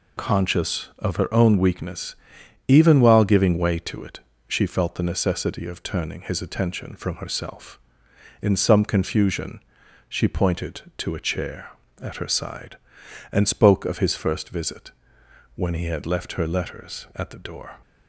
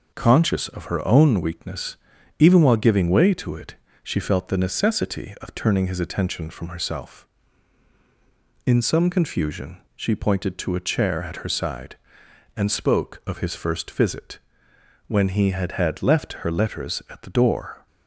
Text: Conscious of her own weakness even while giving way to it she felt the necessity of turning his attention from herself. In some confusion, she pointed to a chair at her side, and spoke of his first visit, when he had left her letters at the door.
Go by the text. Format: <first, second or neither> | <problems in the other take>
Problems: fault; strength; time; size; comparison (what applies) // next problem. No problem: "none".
first | pauses between "weakness" and "even"; at 1.9 s; 0.42 s long; noticeable in the first // pauses between "it" and "she"; slight; at 3.7 s; 0.26 s long; slight in the first // says "had" twice; at 15.7 s